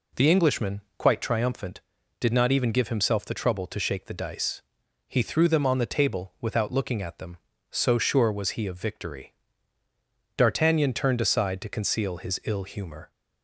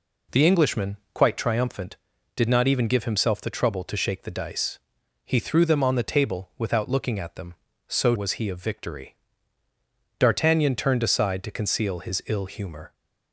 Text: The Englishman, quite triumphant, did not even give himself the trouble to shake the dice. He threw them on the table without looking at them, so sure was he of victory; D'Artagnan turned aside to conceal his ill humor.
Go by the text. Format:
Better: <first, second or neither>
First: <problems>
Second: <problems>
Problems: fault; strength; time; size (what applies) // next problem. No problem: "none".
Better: first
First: none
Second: skips "sure"; at 8.1 s